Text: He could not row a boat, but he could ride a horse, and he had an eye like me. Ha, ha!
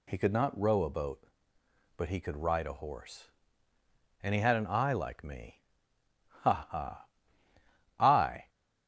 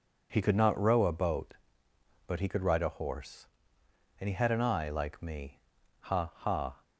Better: second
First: goes on to say "I"; from 7.9 s on; 0.50 s long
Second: none

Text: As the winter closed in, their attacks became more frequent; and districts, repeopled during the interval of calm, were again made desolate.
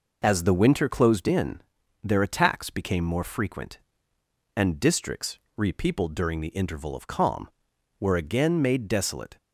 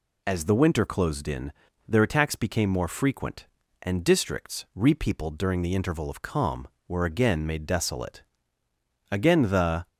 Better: first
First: none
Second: goes on to say "Again the"; noticeable; from 9.0 s on; 0.78 s long

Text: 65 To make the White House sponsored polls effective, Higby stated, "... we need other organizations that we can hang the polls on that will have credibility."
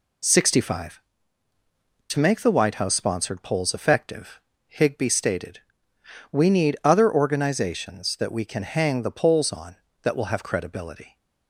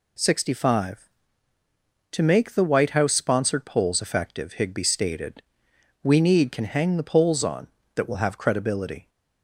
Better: first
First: none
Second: skips "other organizations that we"; at 6.5 s

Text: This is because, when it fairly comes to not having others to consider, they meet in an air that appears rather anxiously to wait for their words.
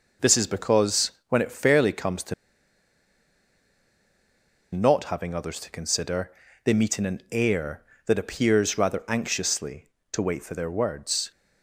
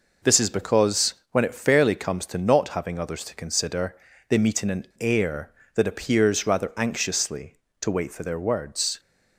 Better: second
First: pauses between "to" and "not"; strong; at 2.3 s; 2.3 s long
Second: none

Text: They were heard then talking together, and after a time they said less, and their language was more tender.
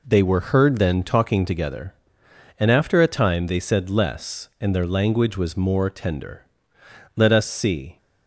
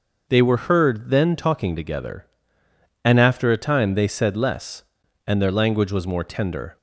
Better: second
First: goes on to say "Let us see"; noticeable; from 7.1 s on; 0.80 s long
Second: none

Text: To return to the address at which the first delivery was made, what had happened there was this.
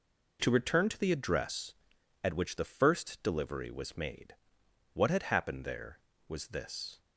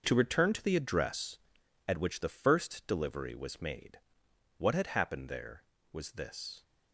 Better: first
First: none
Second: gets quieter; strong; throughout; 11 dB

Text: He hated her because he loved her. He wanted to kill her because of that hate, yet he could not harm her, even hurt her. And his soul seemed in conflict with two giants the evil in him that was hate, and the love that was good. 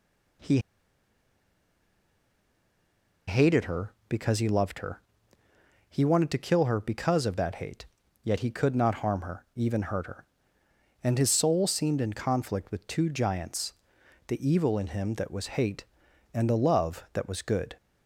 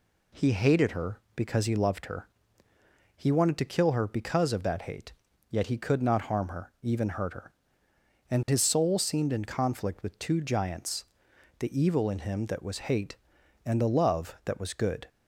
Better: second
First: pauses between "He" and "hated"; strong; at 0.5 s; 2.6 s long // pauses between "giants" and "the"; noticeable; at 13.7 s; 0.54 s long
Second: pauses between "giants" and "the"; noticeable; at 11.0 s; 0.54 s long

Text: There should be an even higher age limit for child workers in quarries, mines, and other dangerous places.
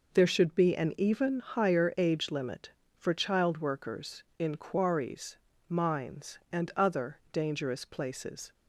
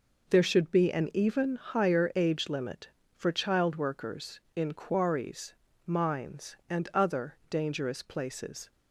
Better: neither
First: none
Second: none

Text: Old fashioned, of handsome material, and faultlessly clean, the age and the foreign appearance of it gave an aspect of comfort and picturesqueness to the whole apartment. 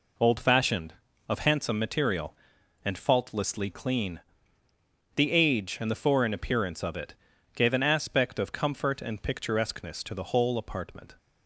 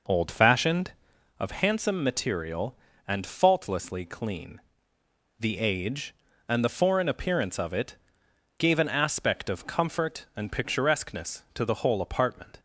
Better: first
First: pauses between "it" and "gave"; at 7.1 s; 0.40 s long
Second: starts louder than the rest; noticeable; until 1.2 s; 5.5 dB // pauses between "it" and "gave"; noticeable; at 7.9 s; 0.62 s long

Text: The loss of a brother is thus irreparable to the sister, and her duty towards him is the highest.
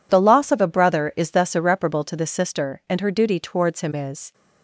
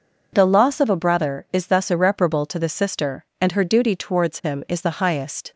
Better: second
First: stops before "the highest"; at 4.3 s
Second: none

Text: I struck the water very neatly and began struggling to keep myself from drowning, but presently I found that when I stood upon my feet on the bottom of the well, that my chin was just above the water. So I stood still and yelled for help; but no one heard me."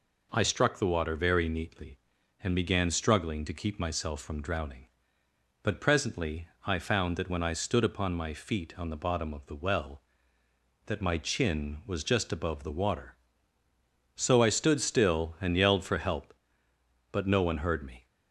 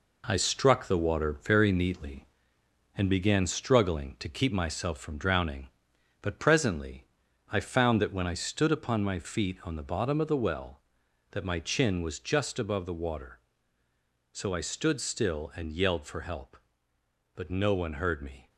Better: first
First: pauses between "presently" and "I"; slight; at 6.4 s; 0.20 s long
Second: gets quieter; throughout; 7 dB // pauses between "presently" and "I"; noticeable; at 7.0 s; 0.48 s long

